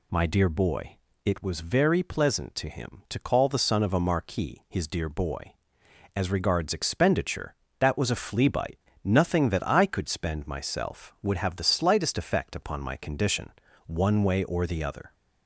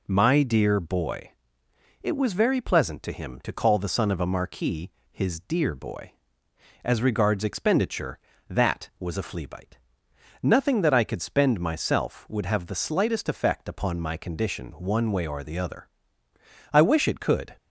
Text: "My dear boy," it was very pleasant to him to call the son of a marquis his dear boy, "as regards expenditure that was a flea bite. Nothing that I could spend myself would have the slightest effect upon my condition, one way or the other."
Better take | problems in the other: first | pauses between "marquis" and "his"; slight; at 4.9 s; 0.20 s long // goes on to say "I wish it could"; noticeable; from 16.7 s on; 0.84 s long

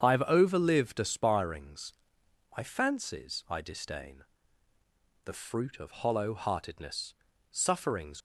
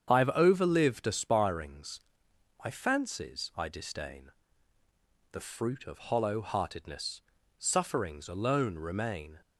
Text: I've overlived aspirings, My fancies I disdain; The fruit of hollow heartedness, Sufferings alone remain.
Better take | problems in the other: second | starts louder than the rest; strong; until 1.0 s; 7.5 dB; strong in the second // stops before "alone remain"; at 8.1 s

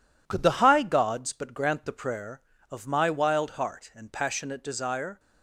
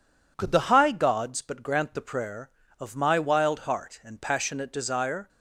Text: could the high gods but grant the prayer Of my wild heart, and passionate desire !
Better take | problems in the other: second | gets quieter; noticeable; throughout; 5.5 dB

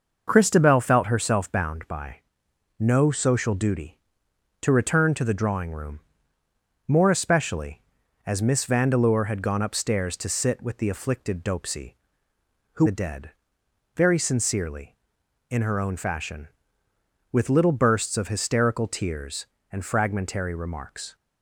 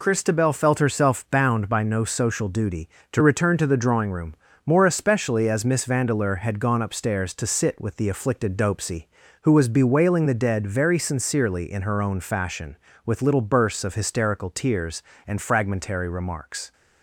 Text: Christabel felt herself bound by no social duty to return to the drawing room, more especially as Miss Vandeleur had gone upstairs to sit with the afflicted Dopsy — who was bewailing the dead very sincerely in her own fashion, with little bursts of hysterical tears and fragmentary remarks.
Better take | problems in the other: second | pauses between "by" and "no"; noticeable; at 2.1 s; 0.62 s long // skips "was bewailing"; at 12.8 s // pauses between "dead" and "very"; noticeable; at 13.2 s; 0.66 s long

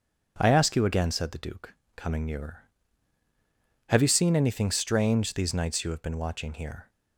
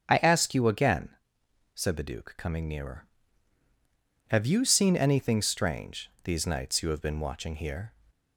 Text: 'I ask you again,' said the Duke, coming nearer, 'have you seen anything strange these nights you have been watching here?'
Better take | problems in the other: neither | starts louder than the rest; the same in both

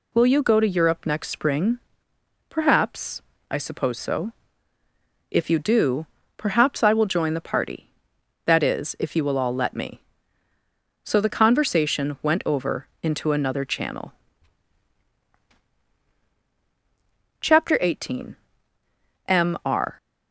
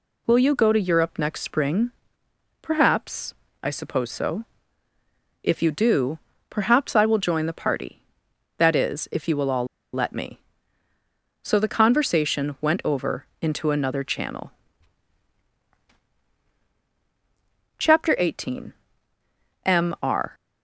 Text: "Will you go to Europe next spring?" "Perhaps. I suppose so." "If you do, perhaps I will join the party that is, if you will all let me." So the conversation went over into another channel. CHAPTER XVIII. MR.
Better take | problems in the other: first | pauses between "all" and "let"; slight; at 9.6 s; 0.27 s long

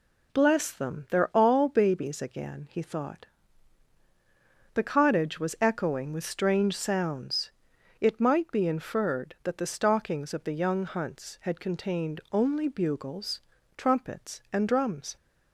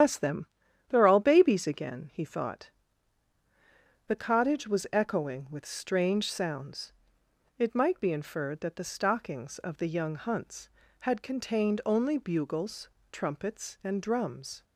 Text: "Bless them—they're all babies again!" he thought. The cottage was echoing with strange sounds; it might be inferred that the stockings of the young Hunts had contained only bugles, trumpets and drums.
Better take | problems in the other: first | loses the start of "Bless"; at 0.0 s; 125 ms // starts louder than the rest; strong; until 1.4 s; 9.5 dB

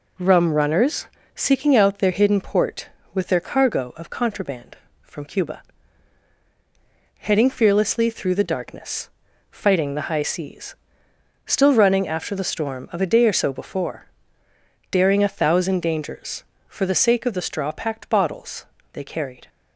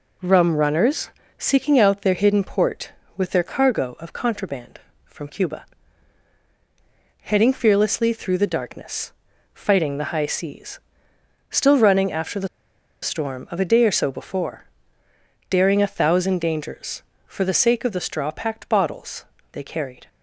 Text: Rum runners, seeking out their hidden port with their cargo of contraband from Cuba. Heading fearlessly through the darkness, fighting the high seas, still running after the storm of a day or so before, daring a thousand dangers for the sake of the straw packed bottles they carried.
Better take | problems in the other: first | pauses between "the" and "storm"; noticeable; at 12.4 s; 0.55 s long // pauses between "bottles" and "they"; slight; at 19.2 s; 0.26 s long; slight in the first

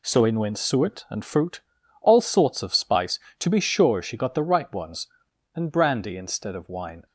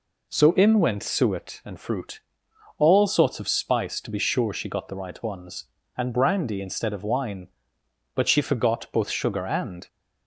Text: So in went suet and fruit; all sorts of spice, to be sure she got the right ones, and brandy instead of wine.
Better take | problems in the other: first | goes on to say "But she forgot both sugar and"; strong; from 8.1 s on; 1.7 s long

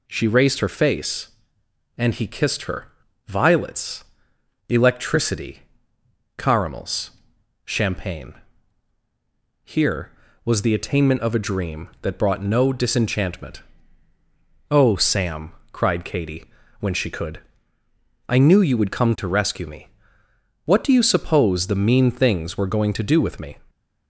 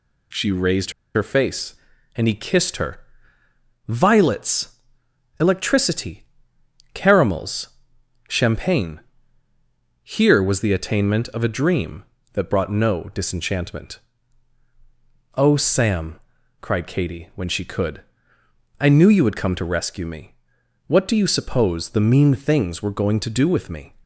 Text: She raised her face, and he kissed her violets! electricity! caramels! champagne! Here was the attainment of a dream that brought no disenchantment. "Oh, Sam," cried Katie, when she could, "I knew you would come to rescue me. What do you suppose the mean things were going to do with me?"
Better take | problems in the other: first | pauses between "raised" and "her"; slight; at 0.9 s; 0.23 s long // pauses between "her" and "violets"; noticeable; at 2.9 s; 0.88 s long; also in the first

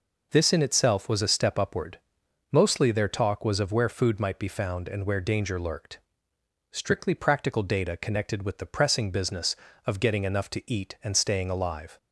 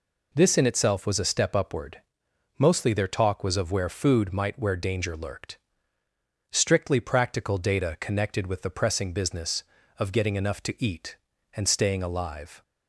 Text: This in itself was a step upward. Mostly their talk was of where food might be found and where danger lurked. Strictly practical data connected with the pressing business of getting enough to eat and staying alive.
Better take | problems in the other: first | skips "be found and"; at 4.5 s

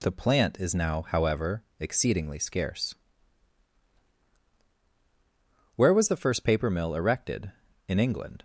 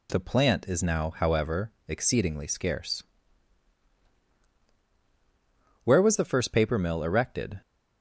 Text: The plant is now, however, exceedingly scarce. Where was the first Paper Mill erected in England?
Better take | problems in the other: first | stops before "in England"; at 7.6 s

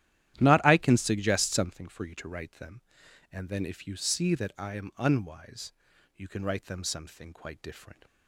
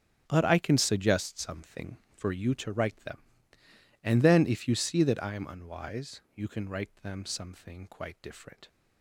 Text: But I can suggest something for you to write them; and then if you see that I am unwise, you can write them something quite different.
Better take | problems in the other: second | starts louder than the rest; strong; until 1.4 s; 12 dB; strong in the second // says "Not" for "But"; at 0.3 s

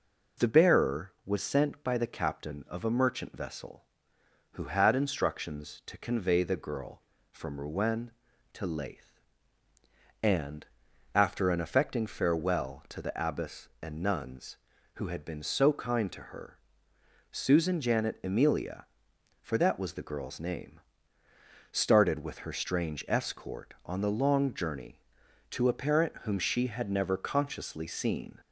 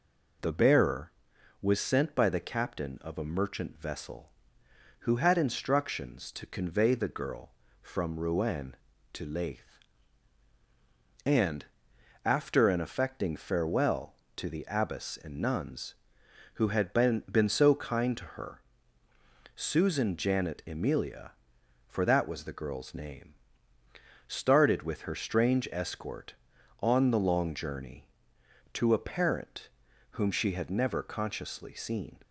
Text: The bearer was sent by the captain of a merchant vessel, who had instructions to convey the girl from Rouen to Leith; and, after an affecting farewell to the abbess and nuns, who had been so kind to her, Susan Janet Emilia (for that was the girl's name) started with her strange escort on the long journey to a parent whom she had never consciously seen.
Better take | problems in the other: first | says "been" twice; at 17.3 s // pauses between "parent" and "whom"; at 29.6 s; 0.42 s long

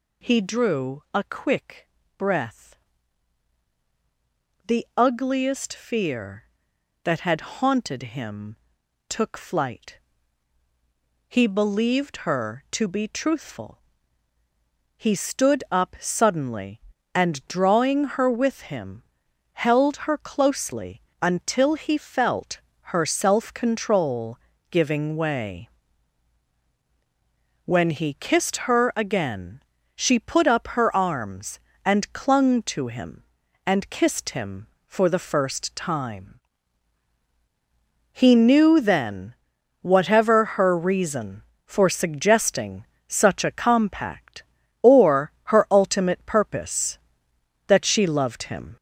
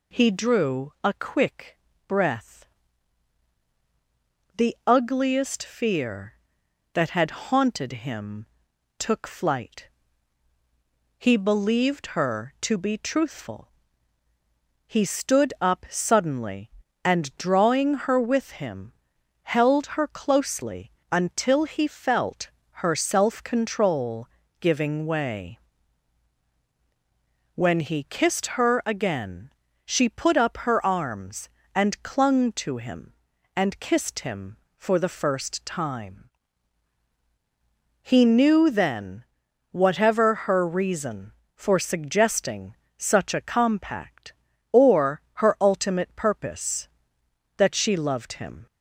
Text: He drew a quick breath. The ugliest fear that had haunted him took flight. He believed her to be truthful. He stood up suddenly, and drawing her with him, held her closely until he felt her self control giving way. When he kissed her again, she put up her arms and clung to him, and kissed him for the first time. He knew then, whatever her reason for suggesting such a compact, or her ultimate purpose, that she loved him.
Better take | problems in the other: second | gets louder; noticeable; throughout; 4.5 dB // pauses between "quick" and "breath"; slight; at 1.8 s; 0.28 s long; slight in the second // pauses between "him" and "took"; noticeable; at 8.5 s; 0.54 s long; noticeable in the second // pauses between "closely" and "until"; slight; at 21.0 s; 0.18 s long; slight in the second // pauses between "felt" and "her"; slight; at 22.6 s; 0.34 s long; slight in the second // pauses between "control" and "giving"; slight; at 24.3 s; 0.34 s long; slight in the second // pauses between "suggesting" and "such"; slight; at 42.8 s; 0.22 s long; slight in the second

